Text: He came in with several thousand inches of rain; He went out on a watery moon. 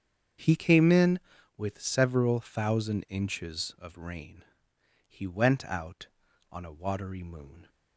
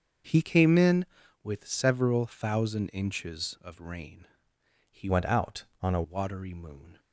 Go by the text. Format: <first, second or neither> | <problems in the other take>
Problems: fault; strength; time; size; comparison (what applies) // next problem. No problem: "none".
first | starts louder than the rest; until 1.6 s; 6.5 dB; strong in the first // changes voice from "went" to "a"; from 5.0 to 6.0 s; 1.0 s long